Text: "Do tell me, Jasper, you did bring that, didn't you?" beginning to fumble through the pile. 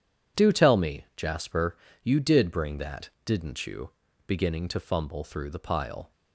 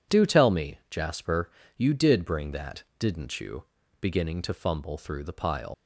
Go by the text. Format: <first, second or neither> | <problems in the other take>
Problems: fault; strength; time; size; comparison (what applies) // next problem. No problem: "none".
first | leaves "pile" unfinished; at 5.7 s; 110 ms